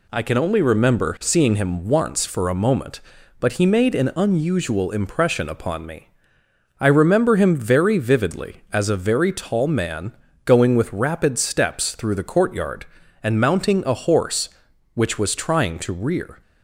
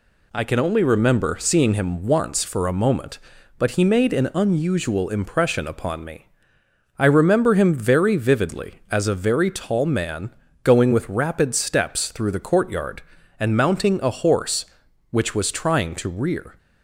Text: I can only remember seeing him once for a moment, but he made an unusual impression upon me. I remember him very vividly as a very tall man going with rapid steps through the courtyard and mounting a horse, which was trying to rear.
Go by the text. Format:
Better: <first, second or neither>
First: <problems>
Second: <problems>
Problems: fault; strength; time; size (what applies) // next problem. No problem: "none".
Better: neither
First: pauses between "man" and "going"; slight; at 10.1 s; 0.30 s long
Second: pauses between "man" and "going"; slight; at 10.3 s; 0.30 s long